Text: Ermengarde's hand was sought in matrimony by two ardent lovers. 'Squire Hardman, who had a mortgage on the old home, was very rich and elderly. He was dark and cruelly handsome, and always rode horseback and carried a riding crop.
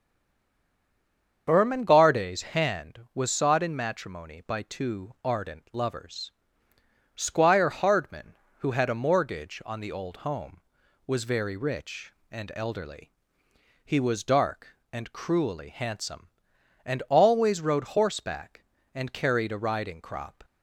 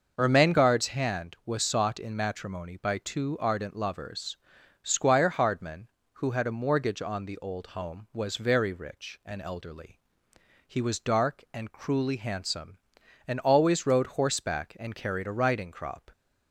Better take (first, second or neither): second